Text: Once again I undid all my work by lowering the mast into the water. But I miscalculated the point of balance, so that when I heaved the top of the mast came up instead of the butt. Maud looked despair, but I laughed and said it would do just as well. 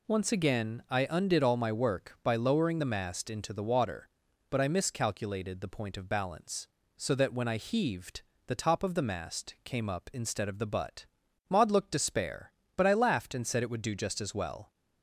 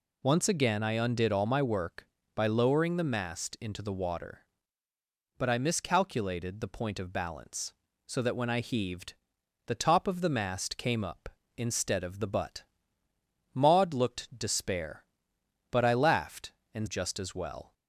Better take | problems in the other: first | pauses between "heaved" and "the"; noticeable; at 9.1 s; 0.54 s long; slight in the first // skips "said it would do"; at 16.8 s

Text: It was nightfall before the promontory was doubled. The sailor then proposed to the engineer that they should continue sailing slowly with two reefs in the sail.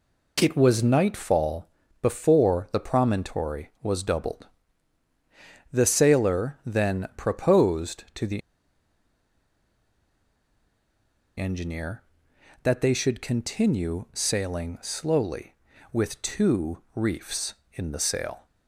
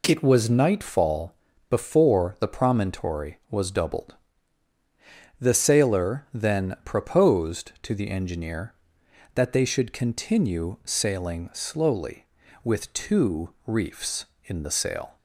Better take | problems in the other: second | pauses between "nightfall" and "before"; slight; at 1.6 s; 0.34 s long; also in the second // pauses between "the" and "engineer"; strong; at 8.4 s; 2.9 s long // pauses between "two" and "reefs"; slight; at 16.7 s; 0.18 s long; slight in the second

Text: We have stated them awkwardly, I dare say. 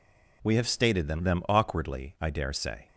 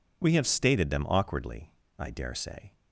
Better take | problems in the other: second | says "them" twice; at 1.2 s

